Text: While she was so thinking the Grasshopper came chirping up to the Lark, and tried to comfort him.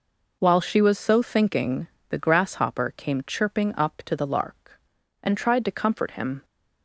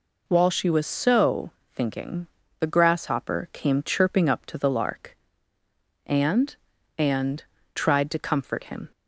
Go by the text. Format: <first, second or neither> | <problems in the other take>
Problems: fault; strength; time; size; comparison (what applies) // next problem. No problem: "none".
first | pauses between "so" and "thinking"; slight; at 1.4 s; 0.24 s long // pauses between "thinking" and "the"; slight; at 2.2 s; 0.32 s long; slight in the first // says "and" twice; at 6.9 s